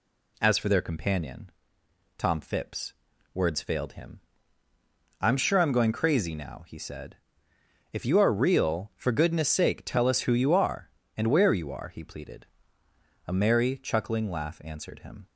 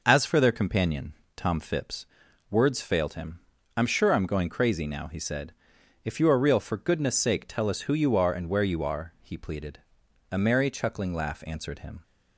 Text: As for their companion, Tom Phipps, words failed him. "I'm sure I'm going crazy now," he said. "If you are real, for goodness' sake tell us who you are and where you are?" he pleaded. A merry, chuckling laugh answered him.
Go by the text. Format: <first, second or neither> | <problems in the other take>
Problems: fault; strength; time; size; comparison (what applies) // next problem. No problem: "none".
neither | none